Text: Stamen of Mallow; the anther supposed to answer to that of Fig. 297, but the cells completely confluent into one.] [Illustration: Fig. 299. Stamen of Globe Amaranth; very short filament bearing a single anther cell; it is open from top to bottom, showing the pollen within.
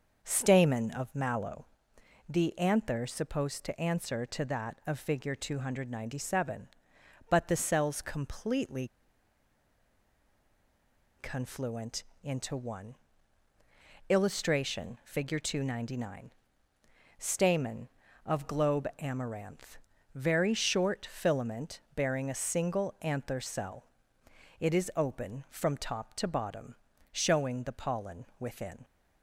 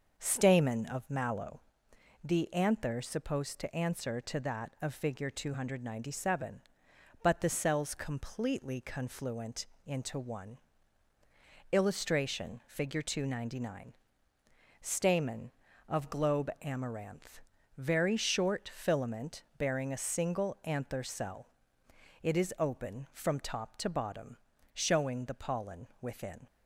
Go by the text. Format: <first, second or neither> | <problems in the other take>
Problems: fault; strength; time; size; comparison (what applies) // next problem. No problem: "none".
second | starts louder than the rest; noticeable; until 1.2 s; 6 dB; noticeable in the second // pauses between "completely" and "confluent"; strong; at 8.8 s; 2.3 s long // pauses between "confluent" and "into"; slight; at 12.0 s; 0.20 s long; slight in the second